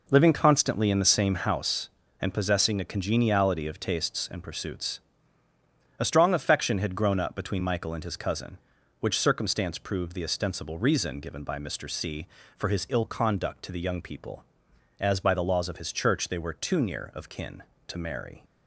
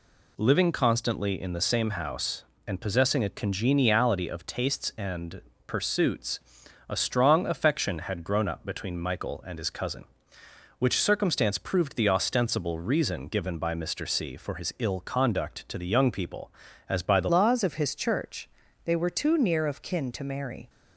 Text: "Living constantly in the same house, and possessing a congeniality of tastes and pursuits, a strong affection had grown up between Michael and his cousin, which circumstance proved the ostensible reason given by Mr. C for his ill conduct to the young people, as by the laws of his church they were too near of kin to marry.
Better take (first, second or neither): first